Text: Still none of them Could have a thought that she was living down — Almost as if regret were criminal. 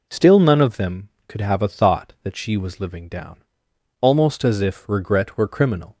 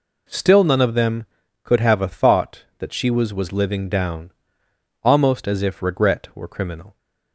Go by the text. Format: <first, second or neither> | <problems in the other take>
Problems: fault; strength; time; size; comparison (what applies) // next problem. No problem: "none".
first | says "was" twice; at 3.3 s